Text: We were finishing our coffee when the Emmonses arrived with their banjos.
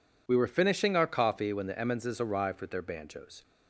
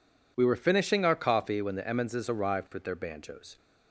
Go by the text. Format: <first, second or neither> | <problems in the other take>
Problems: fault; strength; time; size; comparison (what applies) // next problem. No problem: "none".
neither | none